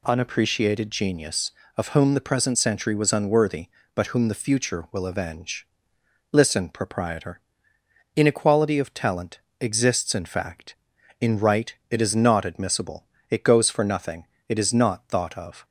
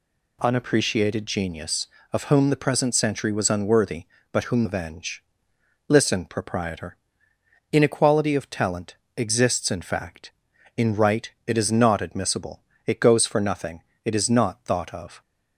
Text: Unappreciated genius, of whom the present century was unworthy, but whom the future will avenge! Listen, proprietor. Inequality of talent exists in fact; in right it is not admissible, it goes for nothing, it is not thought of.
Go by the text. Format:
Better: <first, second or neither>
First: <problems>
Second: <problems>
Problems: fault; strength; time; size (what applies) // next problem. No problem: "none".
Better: first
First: pauses between "talent" and "exists"; slight; at 9.3 s; 0.22 s long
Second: skips "the future will"; at 4.6 s // pauses between "talent" and "exists"; slight; at 8.9 s; 0.22 s long